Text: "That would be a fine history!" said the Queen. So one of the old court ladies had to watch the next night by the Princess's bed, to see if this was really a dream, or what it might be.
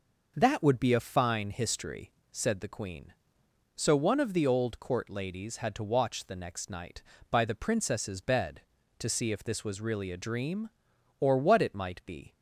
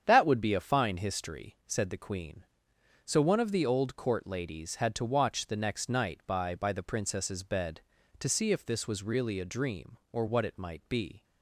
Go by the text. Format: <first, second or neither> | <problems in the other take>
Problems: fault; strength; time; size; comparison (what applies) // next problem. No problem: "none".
first | starts louder than the rest; strong; until 1.0 s; 8 dB // says "by" twice; at 6.5 s